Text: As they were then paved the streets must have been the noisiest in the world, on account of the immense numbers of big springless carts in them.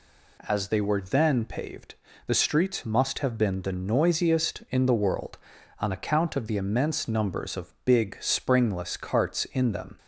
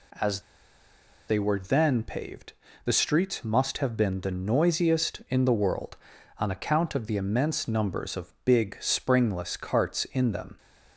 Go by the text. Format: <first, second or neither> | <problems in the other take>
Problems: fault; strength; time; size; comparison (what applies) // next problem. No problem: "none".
first | pauses between "As" and "they"; noticeable; at 0.3 s; 0.88 s long // pauses between "paved" and "the"; slight; at 2.5 s; 0.32 s long; slight in the first